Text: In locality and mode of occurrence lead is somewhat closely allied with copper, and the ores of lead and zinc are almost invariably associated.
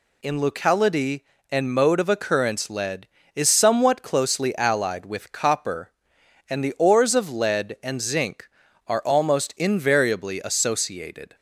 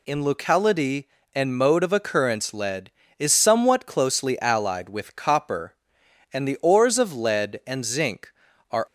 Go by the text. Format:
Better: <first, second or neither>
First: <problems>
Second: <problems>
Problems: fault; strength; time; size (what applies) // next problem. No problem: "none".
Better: first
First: none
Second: stops before "almost invariably associated"; at 8.8 s